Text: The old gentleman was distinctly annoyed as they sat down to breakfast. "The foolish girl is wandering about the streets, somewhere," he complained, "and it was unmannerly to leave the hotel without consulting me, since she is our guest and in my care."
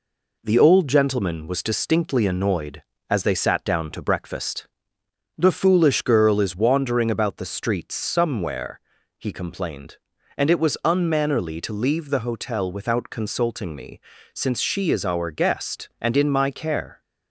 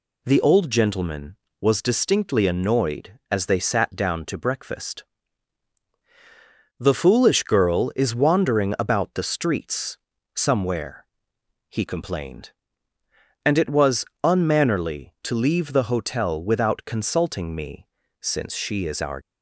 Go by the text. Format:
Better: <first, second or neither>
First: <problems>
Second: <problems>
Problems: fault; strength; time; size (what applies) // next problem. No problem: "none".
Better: first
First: none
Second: pauses between "was" and "unmannerly"; slight; at 14.0 s; 0.18 s long // stops before "guest and in my care"; at 19.2 s